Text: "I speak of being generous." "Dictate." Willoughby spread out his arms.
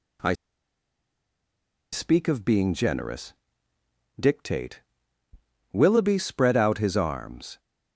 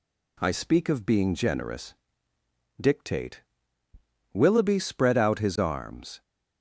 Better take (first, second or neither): second